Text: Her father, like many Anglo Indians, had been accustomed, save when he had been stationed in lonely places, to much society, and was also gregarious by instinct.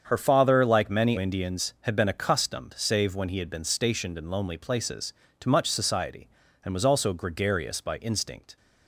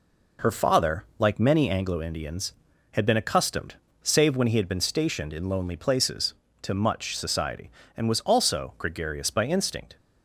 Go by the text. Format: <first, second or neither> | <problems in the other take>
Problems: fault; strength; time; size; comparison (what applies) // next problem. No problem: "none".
second | starts louder than the rest; strong; until 1.0 s; 7.5 dB // skips "Anglo"; at 1.1 s